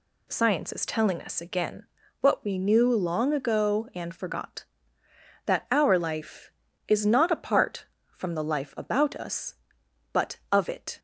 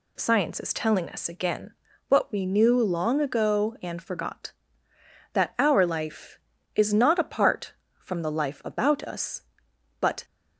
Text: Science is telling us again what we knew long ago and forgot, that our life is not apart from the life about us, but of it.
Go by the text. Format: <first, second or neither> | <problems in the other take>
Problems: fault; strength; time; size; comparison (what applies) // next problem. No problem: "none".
first | pauses between "again" and "what"; slight; at 1.7 s; 0.36 s long; slight in the first // stops before "of it"; at 10.2 s